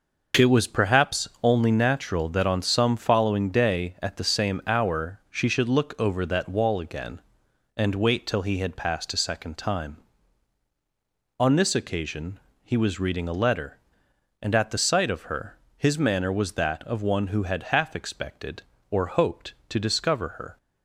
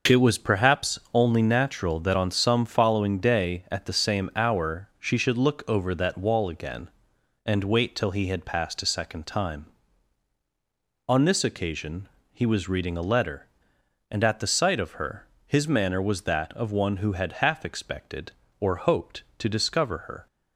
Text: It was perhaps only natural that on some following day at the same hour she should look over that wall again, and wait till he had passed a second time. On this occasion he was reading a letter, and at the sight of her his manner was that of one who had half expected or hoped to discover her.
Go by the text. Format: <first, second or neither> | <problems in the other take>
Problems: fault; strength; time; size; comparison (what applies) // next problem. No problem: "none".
neither | pauses between "occasion" and "he"; slight; the same in both // pauses between "her" and "his"; slight; the same in both